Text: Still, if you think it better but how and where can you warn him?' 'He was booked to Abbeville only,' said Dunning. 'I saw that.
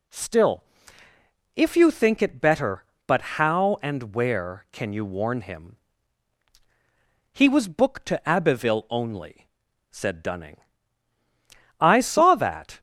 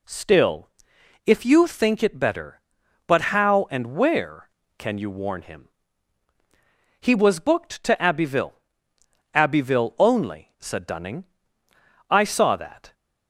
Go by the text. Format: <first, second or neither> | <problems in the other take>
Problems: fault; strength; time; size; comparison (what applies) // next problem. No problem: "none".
first | says "Abbeville" twice; at 9.3 s